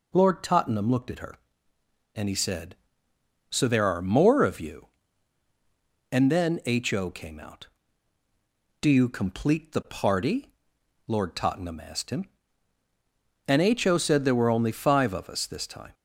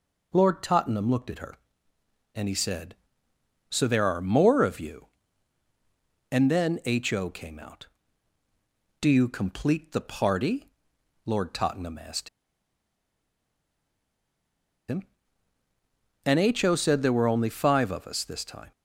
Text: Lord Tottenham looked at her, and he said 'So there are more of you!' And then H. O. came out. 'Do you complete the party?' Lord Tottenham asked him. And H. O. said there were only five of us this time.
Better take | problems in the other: first | pauses between "asked" and "him"; strong; at 12.2 s; 2.6 s long

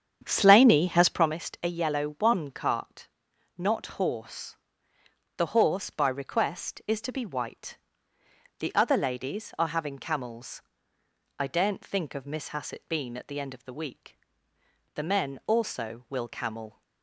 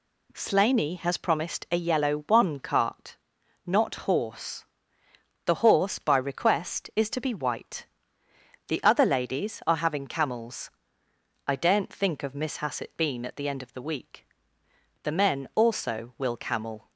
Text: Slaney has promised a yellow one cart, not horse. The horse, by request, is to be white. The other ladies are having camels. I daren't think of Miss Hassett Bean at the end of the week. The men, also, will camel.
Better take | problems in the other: second | starts louder than the rest; strong; until 1.4 s; 8.5 dB

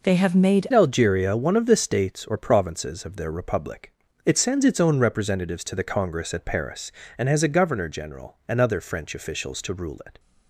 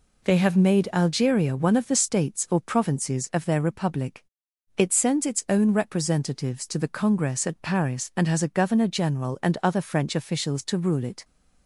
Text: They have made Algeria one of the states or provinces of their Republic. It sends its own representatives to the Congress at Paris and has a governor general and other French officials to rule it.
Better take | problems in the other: second | changes voice at "Algeria"; from 0.7 s on; 9.4 s long

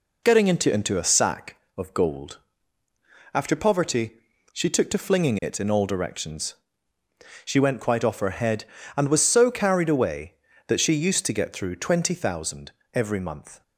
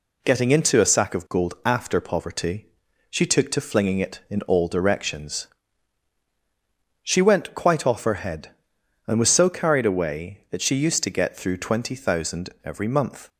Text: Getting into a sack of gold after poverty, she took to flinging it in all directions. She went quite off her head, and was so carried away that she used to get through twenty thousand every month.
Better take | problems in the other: second | says "into" twice; at 0.7 s // pauses between "gold" and "after"; noticeable; at 2.3 s; 0.94 s long // pauses between "thousand" and "every"; slight; at 12.7 s; 0.24 s long; slight in the second

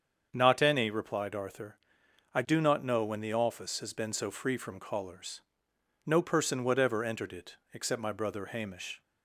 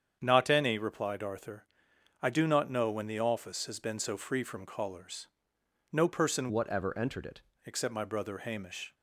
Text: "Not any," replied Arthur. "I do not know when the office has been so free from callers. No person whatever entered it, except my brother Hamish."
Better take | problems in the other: first | starts louder than the rest; strong; until 1.2 s; 8 dB; also in the first // changes voice from "whatever" to "it"; from 6.4 to 7.4 s; 1.0 s long

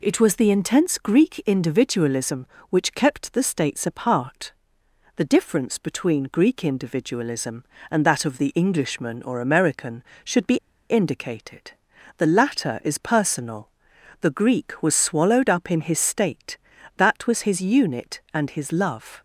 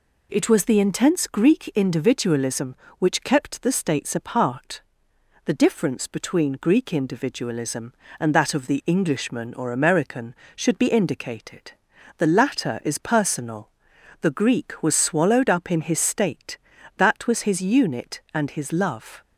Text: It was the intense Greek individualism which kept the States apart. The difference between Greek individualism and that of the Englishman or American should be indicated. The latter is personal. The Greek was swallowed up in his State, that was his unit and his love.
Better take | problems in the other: second | pauses between "be" and "indicated"; slight; at 10.5 s; 0.31 s long

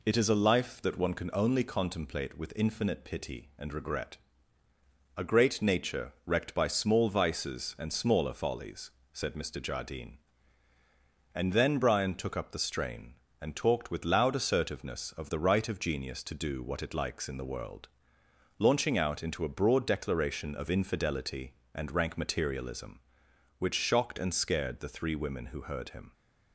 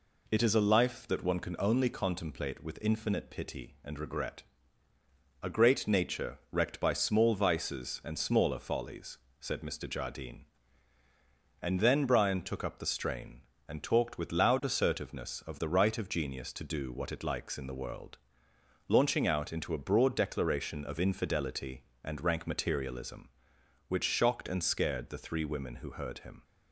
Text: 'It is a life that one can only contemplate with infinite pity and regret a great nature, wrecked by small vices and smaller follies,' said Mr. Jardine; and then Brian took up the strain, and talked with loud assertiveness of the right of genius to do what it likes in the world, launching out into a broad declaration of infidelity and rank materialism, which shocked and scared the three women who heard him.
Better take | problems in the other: neither | pauses between "regret" and "a"; the same in both

